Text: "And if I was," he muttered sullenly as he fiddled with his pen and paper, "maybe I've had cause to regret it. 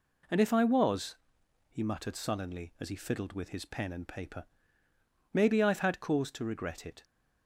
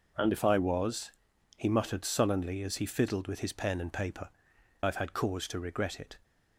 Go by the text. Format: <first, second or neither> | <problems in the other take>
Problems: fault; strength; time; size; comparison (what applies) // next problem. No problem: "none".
first | skips "maybe"; at 4.5 s